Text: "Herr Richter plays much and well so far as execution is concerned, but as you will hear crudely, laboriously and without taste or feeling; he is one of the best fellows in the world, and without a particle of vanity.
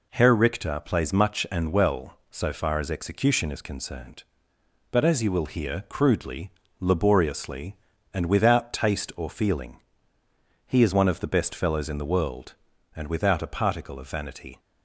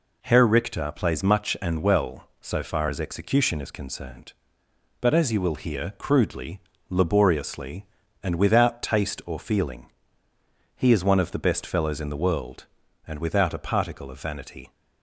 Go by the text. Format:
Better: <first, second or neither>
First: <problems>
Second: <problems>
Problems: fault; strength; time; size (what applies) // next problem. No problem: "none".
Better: neither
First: none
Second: none